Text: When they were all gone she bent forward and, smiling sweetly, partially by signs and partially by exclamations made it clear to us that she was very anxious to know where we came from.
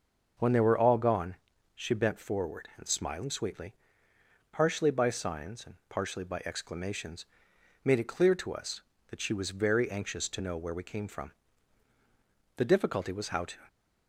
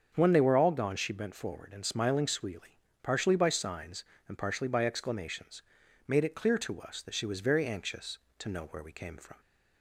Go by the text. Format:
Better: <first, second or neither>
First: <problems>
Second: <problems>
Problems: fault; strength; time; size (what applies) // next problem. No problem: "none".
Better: second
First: starts louder than the rest; until 1.7 s; 6 dB // pauses between "gone" and "she"; at 1.3 s; 0.40 s long // pauses between "exclamations" and "made"; noticeable; at 7.2 s; 0.57 s long // goes on to say "The difficulty was how to"; noticeable; from 12.5 s on; 1.1 s long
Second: starts louder than the rest; until 1.1 s; 6.5 dB // pauses between "exclamations" and "made"; noticeable; at 5.6 s; 0.46 s long